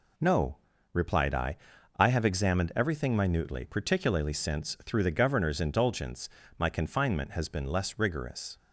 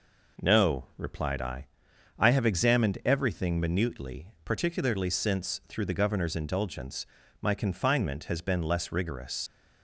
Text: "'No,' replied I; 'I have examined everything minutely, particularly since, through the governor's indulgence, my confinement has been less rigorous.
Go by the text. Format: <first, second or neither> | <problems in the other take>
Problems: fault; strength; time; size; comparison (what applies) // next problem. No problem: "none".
first | leaves "rigorous" unfinished; at 9.4 s; 105 ms